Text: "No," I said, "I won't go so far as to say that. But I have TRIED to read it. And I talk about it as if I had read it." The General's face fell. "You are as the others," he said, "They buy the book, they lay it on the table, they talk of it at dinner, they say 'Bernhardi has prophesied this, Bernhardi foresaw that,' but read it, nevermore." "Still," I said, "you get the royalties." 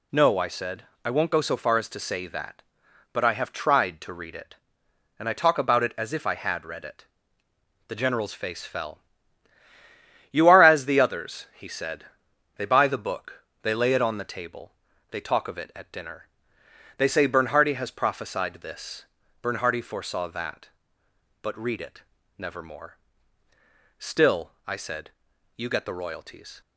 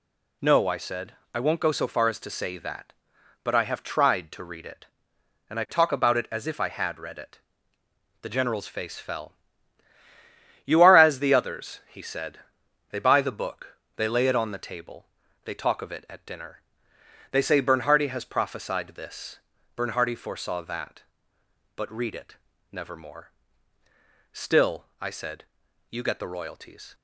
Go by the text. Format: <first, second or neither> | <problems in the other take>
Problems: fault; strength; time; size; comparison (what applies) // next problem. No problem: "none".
neither | none